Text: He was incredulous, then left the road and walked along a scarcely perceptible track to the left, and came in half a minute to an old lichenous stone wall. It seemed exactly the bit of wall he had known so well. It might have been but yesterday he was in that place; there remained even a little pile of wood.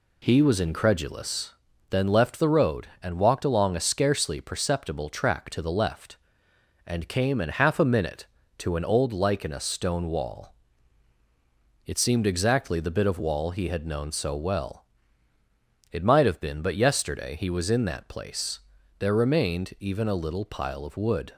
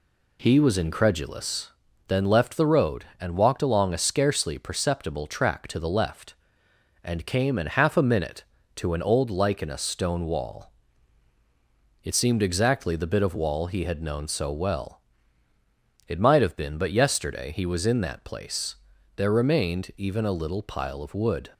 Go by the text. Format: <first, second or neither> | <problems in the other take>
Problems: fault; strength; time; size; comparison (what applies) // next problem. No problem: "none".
neither | none